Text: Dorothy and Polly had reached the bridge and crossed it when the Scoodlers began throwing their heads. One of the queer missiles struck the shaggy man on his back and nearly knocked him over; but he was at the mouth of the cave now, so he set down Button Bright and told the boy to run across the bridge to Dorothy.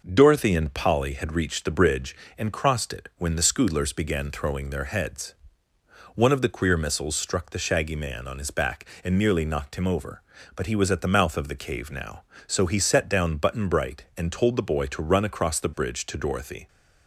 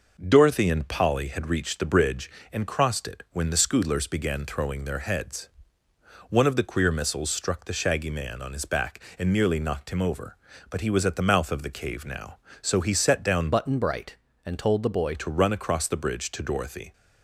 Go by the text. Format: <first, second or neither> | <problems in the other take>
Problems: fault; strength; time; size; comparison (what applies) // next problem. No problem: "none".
first | changes voice from "Button" to "boy"; from 13.5 to 15.1 s; 1.6 s long